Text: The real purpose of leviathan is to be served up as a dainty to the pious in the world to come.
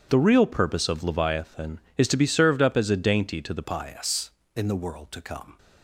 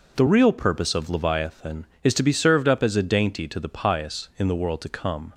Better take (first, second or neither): second